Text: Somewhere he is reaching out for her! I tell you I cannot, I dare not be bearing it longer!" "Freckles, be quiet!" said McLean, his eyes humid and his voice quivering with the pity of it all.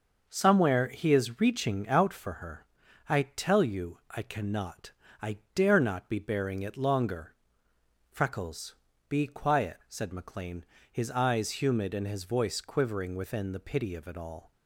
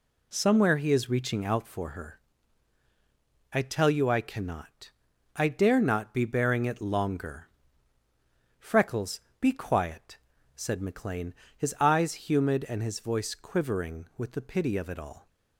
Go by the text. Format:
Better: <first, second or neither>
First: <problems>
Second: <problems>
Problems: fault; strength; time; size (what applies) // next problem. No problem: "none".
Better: second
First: starts louder than the rest; noticeable; until 1.2 s; 6 dB // pauses between "I" and "dare"; slight; at 5.3 s; 0.18 s long // says "within" for "with"; at 13.1 s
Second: none